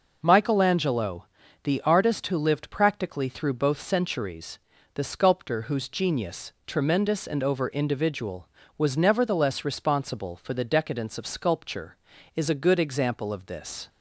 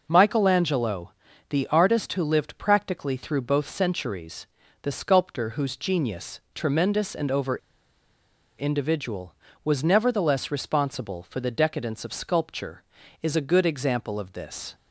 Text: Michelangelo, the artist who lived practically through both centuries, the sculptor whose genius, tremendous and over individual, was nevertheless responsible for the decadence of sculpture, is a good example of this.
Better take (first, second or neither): first